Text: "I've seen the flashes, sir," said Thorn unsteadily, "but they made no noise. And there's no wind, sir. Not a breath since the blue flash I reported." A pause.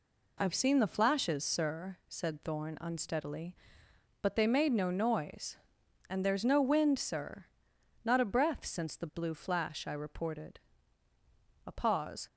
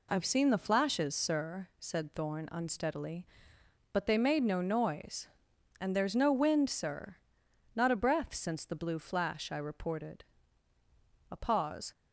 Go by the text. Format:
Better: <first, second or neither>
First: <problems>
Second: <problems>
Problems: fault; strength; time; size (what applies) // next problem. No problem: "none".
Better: neither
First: none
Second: none